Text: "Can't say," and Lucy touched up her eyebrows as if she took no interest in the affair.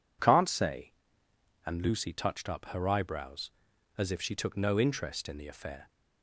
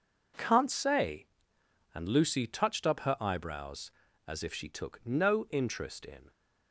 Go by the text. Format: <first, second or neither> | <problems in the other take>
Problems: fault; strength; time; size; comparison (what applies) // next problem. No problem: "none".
first | stops before "the affair"; at 6.3 s